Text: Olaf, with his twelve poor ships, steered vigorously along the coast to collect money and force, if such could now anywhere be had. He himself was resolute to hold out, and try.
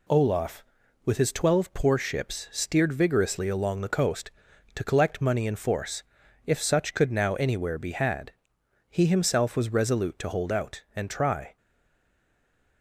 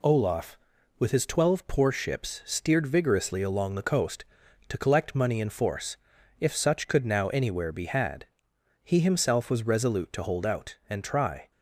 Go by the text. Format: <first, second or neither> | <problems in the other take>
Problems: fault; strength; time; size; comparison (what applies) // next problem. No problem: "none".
second | stays silent after the last word; noticeable; from 11.5 s on; 1.3 s long